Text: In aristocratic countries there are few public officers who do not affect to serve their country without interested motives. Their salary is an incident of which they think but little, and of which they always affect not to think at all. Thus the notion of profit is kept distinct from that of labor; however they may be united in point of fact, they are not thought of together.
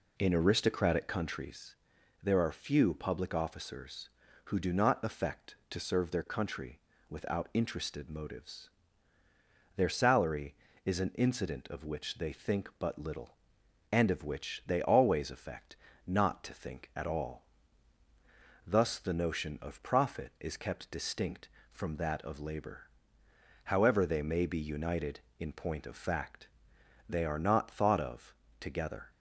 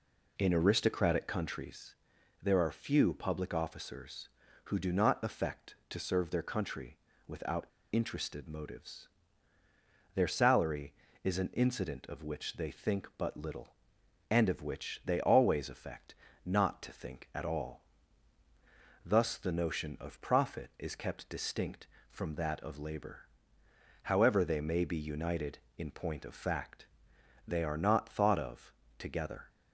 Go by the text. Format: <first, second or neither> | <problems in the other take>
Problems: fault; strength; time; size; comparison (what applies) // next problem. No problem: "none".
first | pauses between "countries" and "there"; noticeable; at 1.9 s; 0.48 s long; noticeable in the first // pauses between "country" and "without"; slight; at 6.9 s; 0.28 s long; slight in the first // pauses between "without" and "interested"; slight; at 7.6 s; 0.26 s long // pauses between "affect" and "not"; slight; at 16.1 s; 0.28 s long; slight in the first // pauses between "of" and "together"; slight; at 28.7 s; 0.24 s long; slight in the first